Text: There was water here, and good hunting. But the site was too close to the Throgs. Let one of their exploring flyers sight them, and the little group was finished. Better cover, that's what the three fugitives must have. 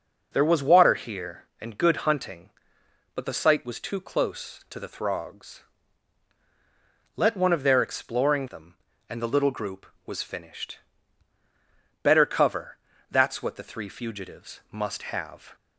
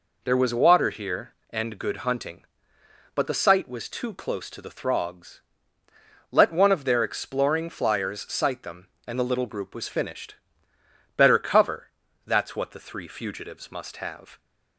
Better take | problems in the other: second | skips "flyers sight"; at 8.4 s

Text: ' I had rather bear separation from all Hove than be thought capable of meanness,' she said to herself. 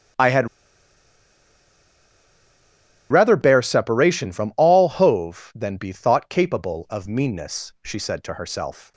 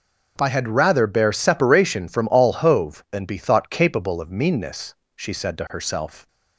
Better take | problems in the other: second | starts louder than the rest; strong; until 3.8 s; 9.5 dB // pauses between "had" and "rather"; strong; at 0.4 s; 2.6 s long

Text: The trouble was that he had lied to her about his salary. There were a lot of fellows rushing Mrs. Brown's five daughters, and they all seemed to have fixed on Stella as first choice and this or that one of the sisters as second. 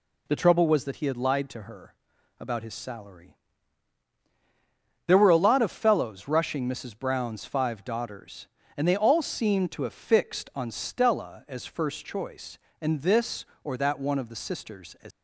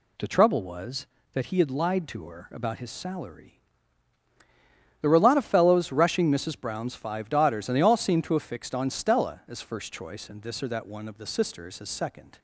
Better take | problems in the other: second | pauses between "her" and "about"; noticeable; at 1.9 s; 0.46 s long // stops before "second"; at 15.1 s

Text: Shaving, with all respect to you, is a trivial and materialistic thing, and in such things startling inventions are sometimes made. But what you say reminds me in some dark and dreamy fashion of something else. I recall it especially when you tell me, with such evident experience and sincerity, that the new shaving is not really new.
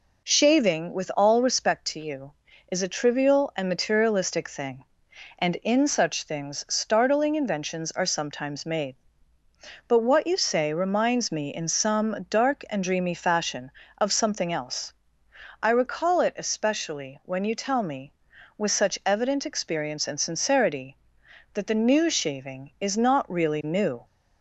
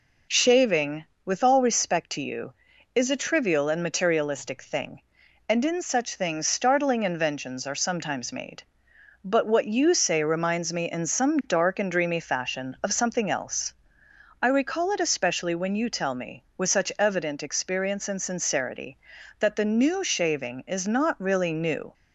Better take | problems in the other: neither | none

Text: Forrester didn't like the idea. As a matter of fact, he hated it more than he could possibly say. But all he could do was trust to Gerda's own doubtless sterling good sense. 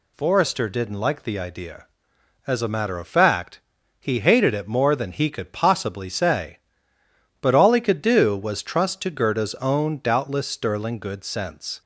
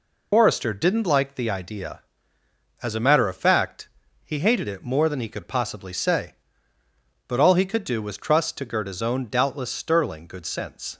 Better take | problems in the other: first | loses the start of "Forrester"; at 0.3 s; 100 ms

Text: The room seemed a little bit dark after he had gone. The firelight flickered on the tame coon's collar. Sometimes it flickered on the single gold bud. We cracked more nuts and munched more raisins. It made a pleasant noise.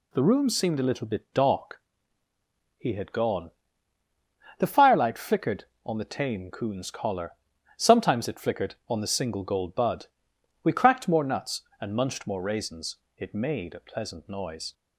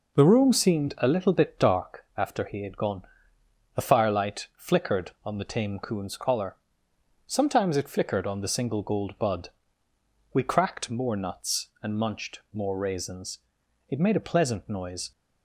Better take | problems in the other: second | skips "after"; at 2.2 s

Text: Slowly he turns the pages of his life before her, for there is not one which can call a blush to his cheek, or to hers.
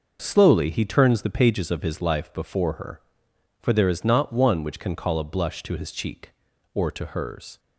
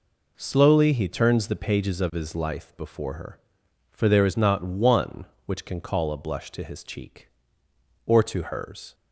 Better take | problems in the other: neither | none

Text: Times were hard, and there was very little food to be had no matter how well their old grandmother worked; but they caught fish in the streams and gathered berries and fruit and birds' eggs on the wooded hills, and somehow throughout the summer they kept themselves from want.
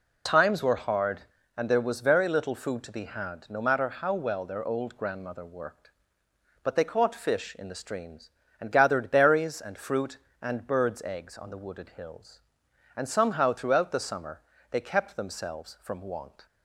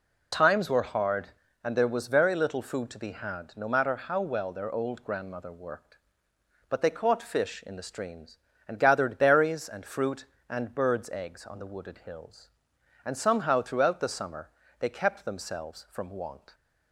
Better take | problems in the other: neither | pauses between "summer" and "they"; slight; the same in both

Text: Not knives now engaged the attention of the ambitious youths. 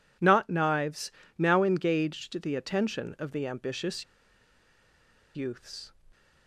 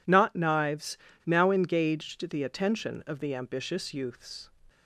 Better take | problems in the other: second | pauses between "knives" and "now"; slight; at 1.0 s; 0.28 s long; slight in the second // pauses between "ambitious" and "youths"; strong; at 4.0 s; 1.3 s long

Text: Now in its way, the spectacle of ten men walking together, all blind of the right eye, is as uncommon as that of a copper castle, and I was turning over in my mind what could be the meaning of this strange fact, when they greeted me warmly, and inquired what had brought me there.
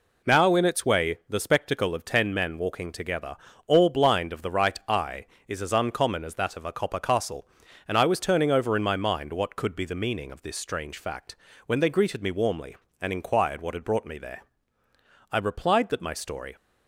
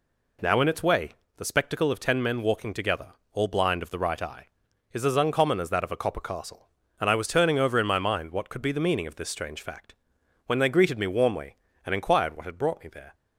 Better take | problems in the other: second | goes on to say "I replied that my story"; noticeable; from 15.3 s on; 1.2 s long

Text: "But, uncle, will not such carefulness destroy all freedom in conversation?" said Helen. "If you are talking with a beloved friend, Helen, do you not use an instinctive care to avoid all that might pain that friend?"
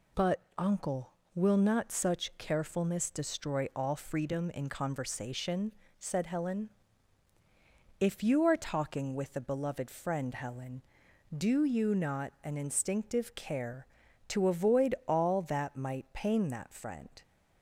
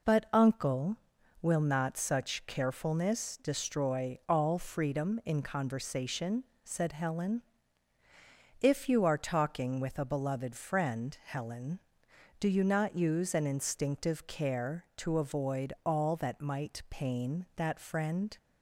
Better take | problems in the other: second | skips "use"; at 12.3 s

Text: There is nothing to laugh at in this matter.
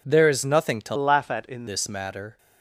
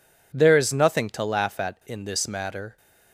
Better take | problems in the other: second | changes voice from "laugh" to "in"; from 0.9 to 1.6 s; 0.7 s long

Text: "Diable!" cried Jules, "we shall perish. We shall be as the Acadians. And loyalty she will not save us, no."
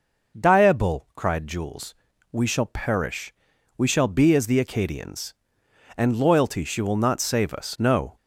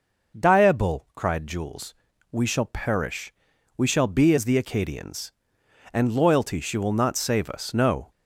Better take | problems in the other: neither | none

